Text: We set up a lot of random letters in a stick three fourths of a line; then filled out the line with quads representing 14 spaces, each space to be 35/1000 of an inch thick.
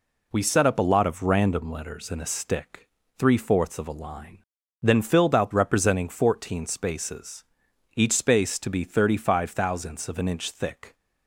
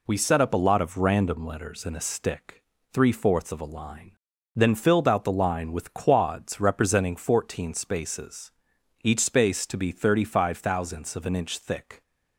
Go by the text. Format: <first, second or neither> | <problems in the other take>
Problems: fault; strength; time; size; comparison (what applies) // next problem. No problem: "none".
second | pauses between "stick" and "three"; slight; at 2.8 s; 0.32 s long; slight in the second // skips "the line with quads"; at 5.5 s